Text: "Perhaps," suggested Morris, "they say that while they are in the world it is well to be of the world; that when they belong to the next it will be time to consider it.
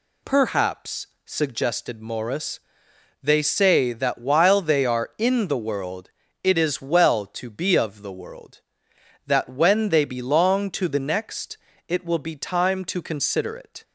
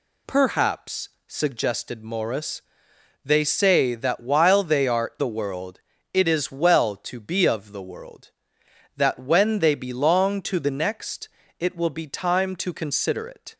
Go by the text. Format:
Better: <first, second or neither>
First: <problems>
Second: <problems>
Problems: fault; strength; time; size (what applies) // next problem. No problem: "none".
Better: first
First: pauses between "world" and "it"; slight; at 6.0 s; 0.32 s long // pauses between "next" and "it"; slight; at 11.5 s; 0.32 s long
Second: skips "in"; at 5.1 s // pauses between "world" and "it"; slight; at 5.7 s; 0.32 s long // pauses between "next" and "it"; slight; at 11.2 s; 0.32 s long